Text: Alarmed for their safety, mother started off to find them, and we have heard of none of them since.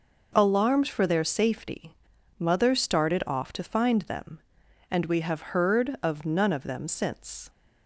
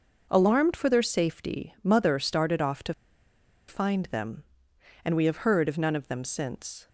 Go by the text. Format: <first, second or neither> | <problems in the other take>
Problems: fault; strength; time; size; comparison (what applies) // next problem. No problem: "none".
first | pauses between "to" and "find"; noticeable; at 2.9 s; 0.74 s long